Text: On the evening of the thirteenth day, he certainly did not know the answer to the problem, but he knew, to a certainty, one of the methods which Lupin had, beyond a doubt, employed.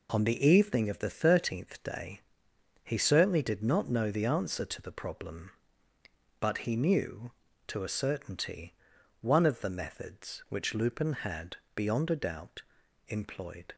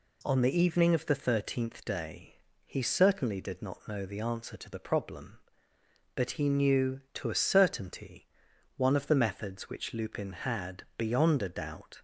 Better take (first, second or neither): first